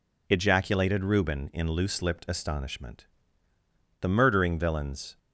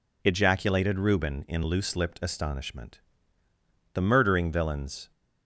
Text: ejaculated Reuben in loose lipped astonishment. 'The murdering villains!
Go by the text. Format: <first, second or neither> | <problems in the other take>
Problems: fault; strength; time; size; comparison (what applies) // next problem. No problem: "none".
neither | none